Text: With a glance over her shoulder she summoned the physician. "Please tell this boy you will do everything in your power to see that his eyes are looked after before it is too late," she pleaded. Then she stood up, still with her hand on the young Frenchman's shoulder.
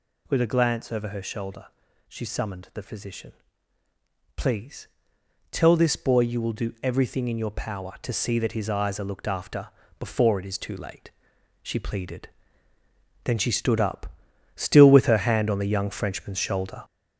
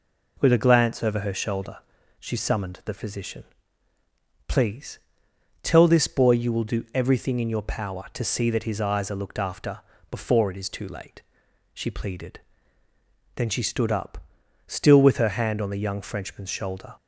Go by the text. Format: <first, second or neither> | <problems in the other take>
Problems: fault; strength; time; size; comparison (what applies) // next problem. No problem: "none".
second | gets louder; noticeable; throughout; 5 dB // pauses between "shoulder" and "she"; at 1.6 s; 0.42 s long; also in the second // pauses between "Please" and "tell"; noticeable; at 4.8 s; 0.64 s long; noticeable in the second // pauses between "after" and "before"; slight; at 9.6 s; 0.32 s long; slight in the second